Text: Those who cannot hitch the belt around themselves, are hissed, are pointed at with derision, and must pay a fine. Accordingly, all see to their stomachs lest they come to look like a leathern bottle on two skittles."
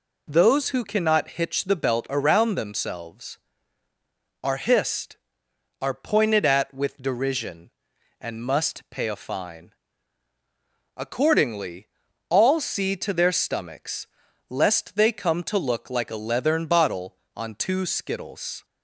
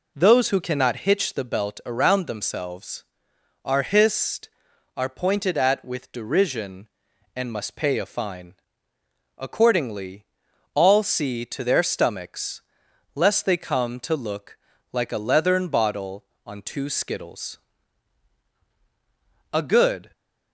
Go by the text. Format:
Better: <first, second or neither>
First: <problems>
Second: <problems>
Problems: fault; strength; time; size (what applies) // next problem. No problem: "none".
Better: first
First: pauses between "stomachs" and "lest"; at 14.0 s; 0.44 s long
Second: pauses between "stomachs" and "lest"; noticeable; at 12.6 s; 0.52 s long // pauses between "look" and "like"; slight; at 14.5 s; 0.36 s long // goes on to say "A good"; from 19.5 s on; 0.60 s long